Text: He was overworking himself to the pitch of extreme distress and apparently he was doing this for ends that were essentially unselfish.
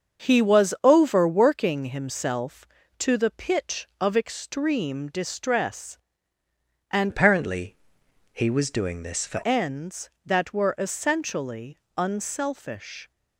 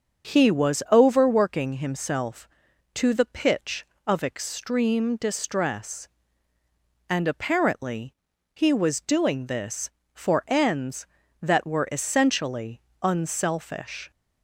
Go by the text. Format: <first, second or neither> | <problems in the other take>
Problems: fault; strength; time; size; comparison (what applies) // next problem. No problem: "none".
second | starts louder than the rest; until 1.3 s; 7 dB; also in the second // changes voice from "apparently" to "for"; from 7.0 to 9.4 s; 2.4 s long // pauses between "apparently" and "he"; noticeable; at 7.7 s; 0.56 s long; also in the second // pauses between "essentially" and "unselfish"; slight; at 11.7 s; 0.18 s long; slight in the second